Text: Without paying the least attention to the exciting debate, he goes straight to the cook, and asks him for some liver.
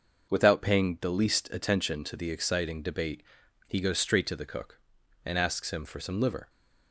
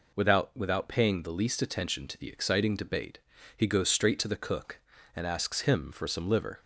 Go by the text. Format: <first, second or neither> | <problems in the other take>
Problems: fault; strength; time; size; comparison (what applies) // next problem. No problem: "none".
first | says "Without" twice; at 0.5 s